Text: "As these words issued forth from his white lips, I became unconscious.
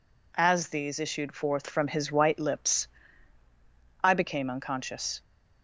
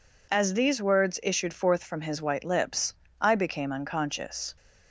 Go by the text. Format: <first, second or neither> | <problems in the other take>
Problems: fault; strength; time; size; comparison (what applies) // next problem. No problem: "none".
second | skips "words"; at 0.9 s